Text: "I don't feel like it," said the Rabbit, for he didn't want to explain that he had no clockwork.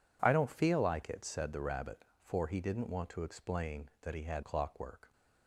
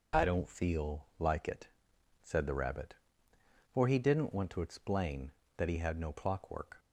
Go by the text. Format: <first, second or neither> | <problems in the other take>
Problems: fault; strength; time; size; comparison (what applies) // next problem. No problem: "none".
second | skips "no"; at 4.4 s